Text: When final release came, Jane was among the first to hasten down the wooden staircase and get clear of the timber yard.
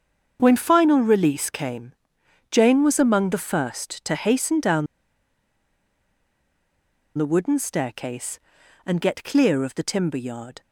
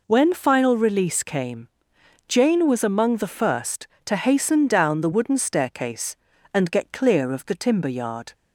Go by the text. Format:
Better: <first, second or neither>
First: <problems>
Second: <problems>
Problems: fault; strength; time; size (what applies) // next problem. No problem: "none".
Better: second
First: starts louder than the rest; until 1.4 s; 7 dB // pauses between "down" and "the"; strong; at 4.8 s; 2.3 s long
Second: none